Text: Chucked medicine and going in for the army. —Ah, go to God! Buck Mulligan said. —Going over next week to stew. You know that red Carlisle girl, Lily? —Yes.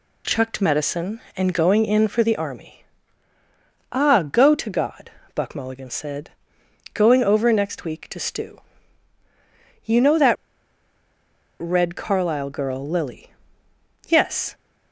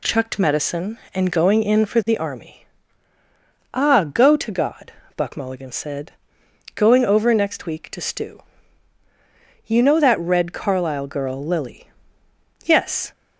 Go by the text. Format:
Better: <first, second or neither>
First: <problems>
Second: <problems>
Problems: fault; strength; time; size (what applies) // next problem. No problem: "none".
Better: second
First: pauses between "that" and "red"; strong; at 10.3 s; 1.2 s long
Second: none